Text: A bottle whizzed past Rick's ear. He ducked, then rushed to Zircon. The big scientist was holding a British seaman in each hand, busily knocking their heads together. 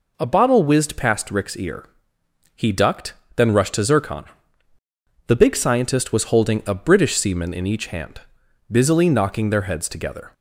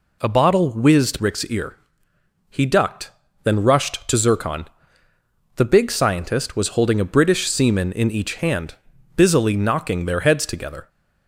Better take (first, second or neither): first